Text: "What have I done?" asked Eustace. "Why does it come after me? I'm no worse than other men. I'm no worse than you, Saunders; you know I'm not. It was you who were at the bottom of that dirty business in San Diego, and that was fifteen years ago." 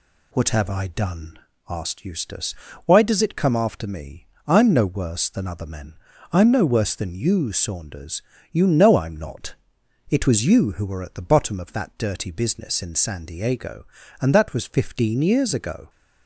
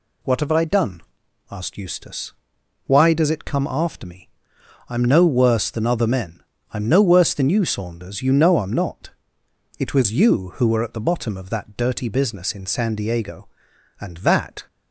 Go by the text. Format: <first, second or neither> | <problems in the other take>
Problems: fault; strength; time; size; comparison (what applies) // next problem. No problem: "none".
first | stops before "was fifteen years ago"; at 14.6 s